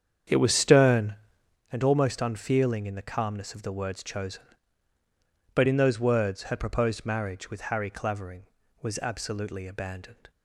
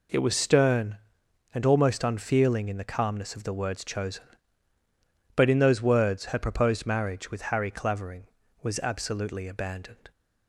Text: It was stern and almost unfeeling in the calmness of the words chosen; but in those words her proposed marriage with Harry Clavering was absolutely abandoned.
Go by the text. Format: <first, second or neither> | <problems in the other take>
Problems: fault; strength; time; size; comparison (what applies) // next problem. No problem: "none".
second | starts louder than the rest; strong; until 1.6 s; 8 dB